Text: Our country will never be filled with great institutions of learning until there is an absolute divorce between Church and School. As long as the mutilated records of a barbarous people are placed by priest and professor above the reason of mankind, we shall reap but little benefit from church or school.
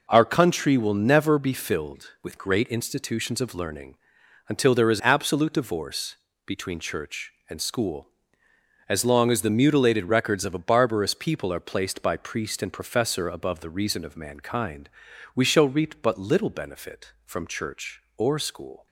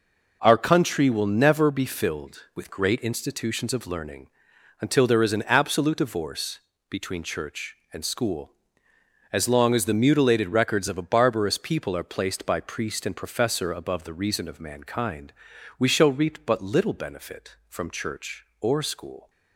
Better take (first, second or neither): second